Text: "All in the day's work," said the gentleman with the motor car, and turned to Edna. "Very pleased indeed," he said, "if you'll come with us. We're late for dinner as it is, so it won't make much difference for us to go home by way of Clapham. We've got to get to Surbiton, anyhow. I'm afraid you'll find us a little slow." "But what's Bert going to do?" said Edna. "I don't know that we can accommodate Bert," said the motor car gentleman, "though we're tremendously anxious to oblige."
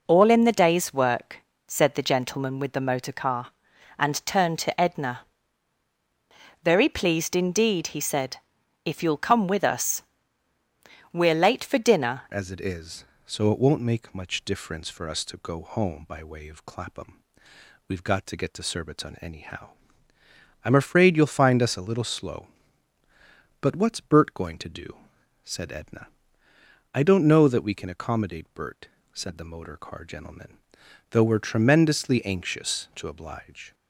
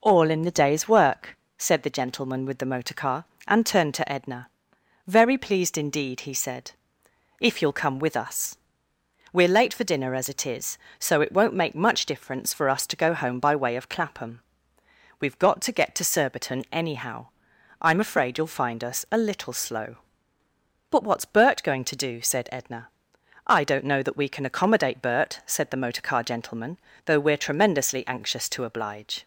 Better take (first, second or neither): second